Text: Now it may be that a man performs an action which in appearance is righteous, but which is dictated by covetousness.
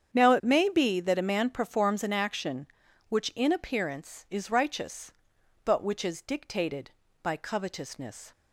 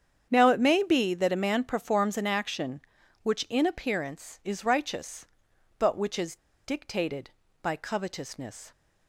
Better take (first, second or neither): first